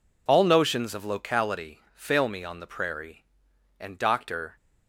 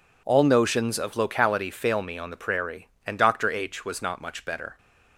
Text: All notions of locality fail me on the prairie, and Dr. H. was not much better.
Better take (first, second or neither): second